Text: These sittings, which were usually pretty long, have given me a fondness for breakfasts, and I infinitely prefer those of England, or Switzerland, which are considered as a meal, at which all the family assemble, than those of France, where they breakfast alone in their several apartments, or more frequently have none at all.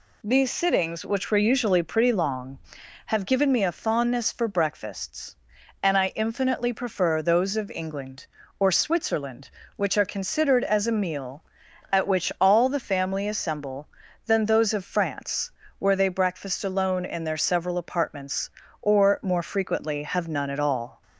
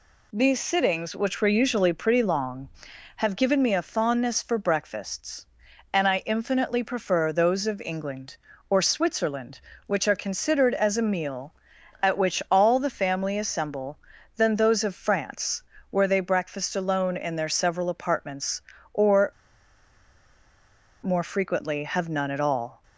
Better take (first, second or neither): first